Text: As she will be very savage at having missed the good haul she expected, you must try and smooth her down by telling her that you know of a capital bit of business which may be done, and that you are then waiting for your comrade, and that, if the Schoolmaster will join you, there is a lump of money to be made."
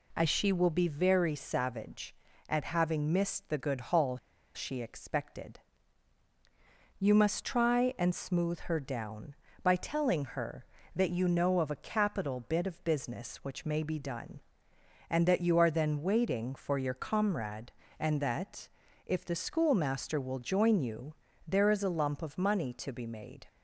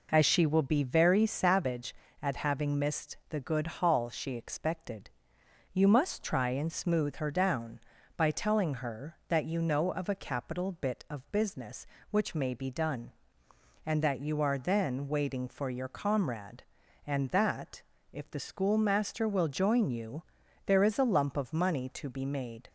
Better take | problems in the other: second | pauses between "haul" and "she"; at 4.1 s; 0.37 s long

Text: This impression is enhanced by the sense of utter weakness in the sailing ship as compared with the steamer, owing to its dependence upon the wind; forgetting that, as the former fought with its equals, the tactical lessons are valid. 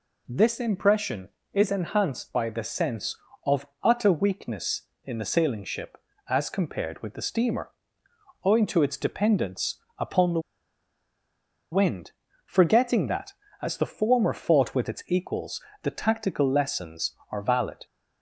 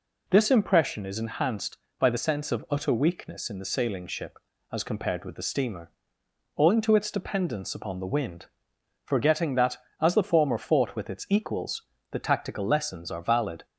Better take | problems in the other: second | pauses between "of" and "utter"; slight; at 3.6 s; 0.16 s long // pauses between "dependence" and "upon"; slight; at 9.7 s; 0.20 s long // pauses between "the" and "wind"; strong; at 10.3 s; 1.3 s long

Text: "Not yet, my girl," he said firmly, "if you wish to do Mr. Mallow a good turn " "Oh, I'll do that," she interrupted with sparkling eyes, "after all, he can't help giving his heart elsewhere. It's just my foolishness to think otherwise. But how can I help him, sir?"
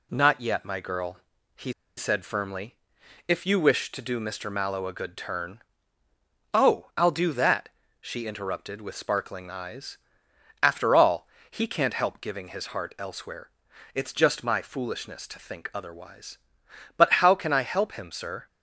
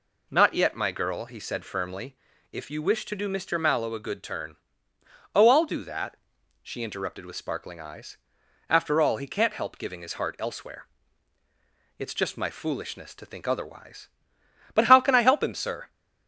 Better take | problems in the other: second | pauses between "he" and "said"; slight; at 1.7 s; 0.25 s long

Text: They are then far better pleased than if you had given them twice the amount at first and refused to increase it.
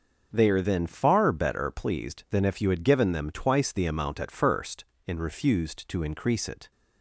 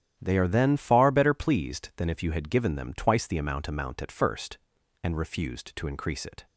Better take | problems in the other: first | starts louder than the rest; strong; until 1.2 s; 10.5 dB; also in the first // says "amount" twice; at 3.6 s

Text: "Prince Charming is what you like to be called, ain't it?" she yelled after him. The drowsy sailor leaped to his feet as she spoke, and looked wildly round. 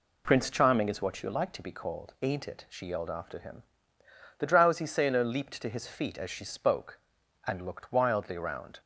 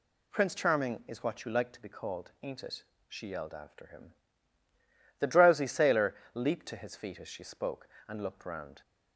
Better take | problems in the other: first | pauses between "sailor" and "leaped"; slight; at 6.1 s; 0.18 s long // skips "wildly"; at 8.4 s

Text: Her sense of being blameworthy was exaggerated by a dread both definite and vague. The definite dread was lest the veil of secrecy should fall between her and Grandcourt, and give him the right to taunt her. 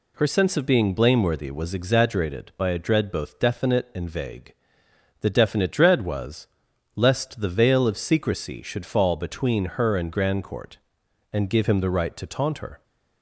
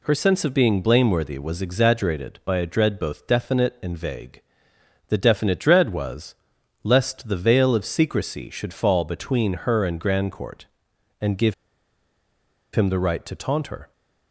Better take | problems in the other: first | pauses between "was" and "lest"; noticeable; at 6.3 s; 0.50 s long; noticeable in the first // pauses between "give" and "him"; at 11.5 s; 1.1 s long

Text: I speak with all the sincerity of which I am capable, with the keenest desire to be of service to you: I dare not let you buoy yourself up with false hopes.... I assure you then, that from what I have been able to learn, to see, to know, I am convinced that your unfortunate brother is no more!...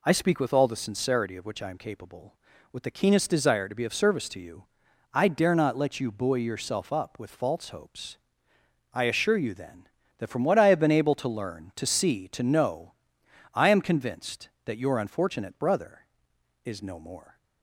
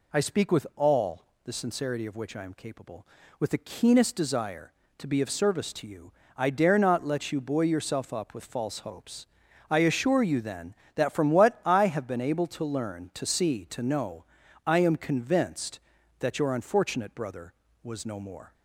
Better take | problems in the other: first | pauses between "all" and "the"; slight; at 1.2 s; 0.22 s long // says "was" for "is"; at 17.8 s

